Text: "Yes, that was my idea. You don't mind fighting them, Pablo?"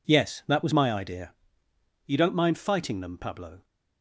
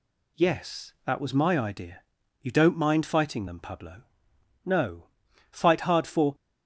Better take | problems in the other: first | goes on to say "No fight hard for"; strong; from 4.6 s on; 1.7 s long

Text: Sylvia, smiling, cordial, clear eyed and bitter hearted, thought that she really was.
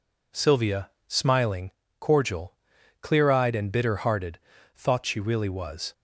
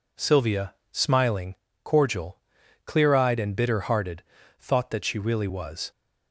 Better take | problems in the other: second | skips "that"; at 5.0 s

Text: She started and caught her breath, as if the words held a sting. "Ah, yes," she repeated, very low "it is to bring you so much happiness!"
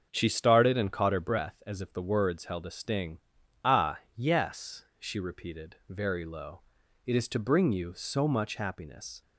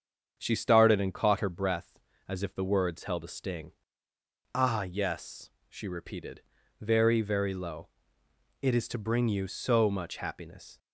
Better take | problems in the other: first | starts louder than the rest; strong; until 1.3 s; 7 dB; also in the first // says "very" twice; at 7.2 s // pauses between "low" and "it"; noticeable; at 7.8 s; 0.74 s long; also in the first

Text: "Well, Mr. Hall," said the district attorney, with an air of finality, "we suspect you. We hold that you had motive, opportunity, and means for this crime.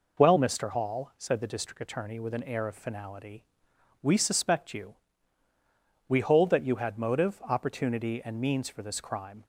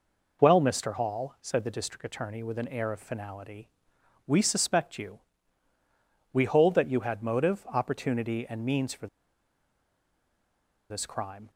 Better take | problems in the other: first | pauses between "for" and "this"; strong; at 9.0 s; 1.8 s long

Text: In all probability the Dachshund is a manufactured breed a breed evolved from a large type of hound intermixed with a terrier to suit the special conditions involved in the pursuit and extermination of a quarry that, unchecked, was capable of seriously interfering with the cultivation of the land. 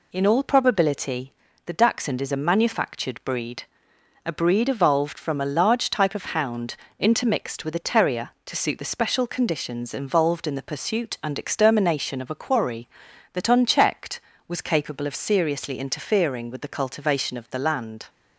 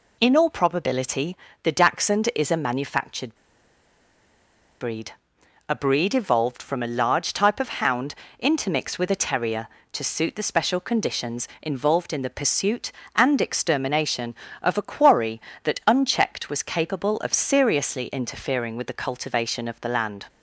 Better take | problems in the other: first | pauses between "probability" and "the"; slight; at 1.3 s; 0.26 s long; slight in the first // pauses between "manufactured" and "breed"; strong; at 3.3 s; 1.4 s long // pauses between "breed" and "a"; noticeable; at 5.1 s; 0.56 s long; noticeable in the first // pauses between "hound" and "intermixed"; slight; at 8.1 s; 0.26 s long; slight in the first

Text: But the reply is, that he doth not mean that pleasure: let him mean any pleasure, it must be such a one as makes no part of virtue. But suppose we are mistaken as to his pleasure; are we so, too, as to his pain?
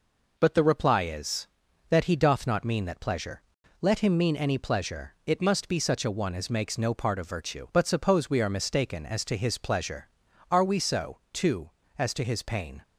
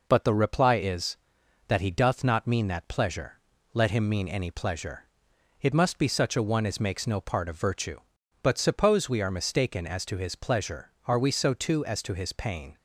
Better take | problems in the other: neither | none

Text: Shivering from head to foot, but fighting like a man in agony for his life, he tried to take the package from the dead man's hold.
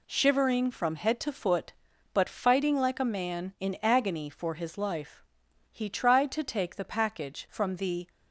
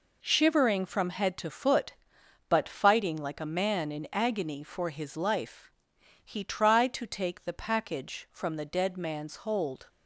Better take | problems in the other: second | stops before "dead man's hold"; at 8.0 s

